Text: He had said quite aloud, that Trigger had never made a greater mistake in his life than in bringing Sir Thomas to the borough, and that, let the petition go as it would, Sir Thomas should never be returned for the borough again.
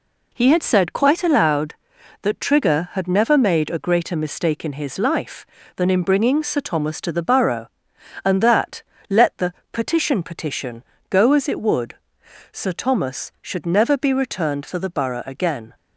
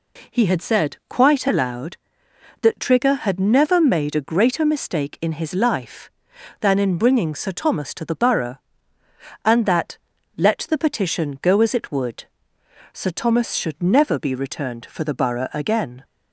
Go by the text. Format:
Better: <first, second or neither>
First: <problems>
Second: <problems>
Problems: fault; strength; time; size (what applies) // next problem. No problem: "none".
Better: second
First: pauses between "the" and "petition"; slight; at 9.5 s; 0.20 s long // says "petition" twice; at 10.2 s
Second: none